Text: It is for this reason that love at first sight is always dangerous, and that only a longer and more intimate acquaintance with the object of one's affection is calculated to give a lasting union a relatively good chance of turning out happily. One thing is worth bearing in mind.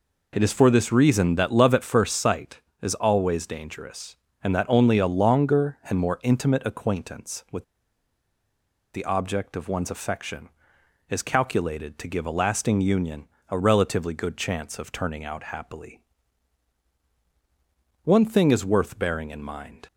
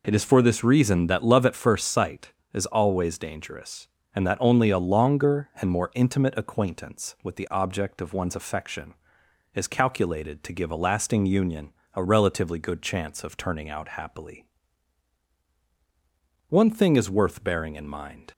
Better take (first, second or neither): second